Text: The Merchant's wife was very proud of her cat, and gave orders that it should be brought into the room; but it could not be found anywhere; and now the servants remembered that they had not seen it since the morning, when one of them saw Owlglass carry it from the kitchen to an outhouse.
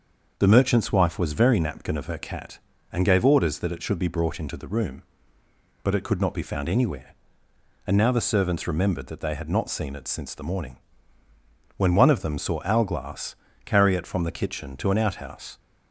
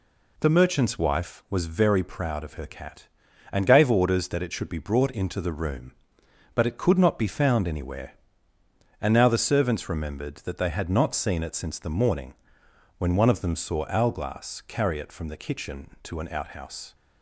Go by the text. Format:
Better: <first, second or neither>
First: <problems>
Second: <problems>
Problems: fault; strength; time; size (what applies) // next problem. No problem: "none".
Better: second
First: starts louder than the rest; until 1.3 s; 6 dB // says "napkin" for "proud"; at 1.6 s // pauses between "Owlglass" and "carry"; slight; at 13.3 s; 0.32 s long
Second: none